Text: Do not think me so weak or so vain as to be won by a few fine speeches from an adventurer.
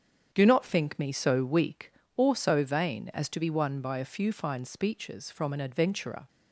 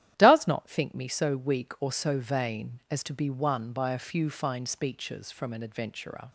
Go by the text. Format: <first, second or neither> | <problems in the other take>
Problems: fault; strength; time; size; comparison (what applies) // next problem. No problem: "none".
first | starts louder than the rest; strong; until 1.1 s; 11.5 dB; strong in the first // says "Does" for "Do"; at 0.1 s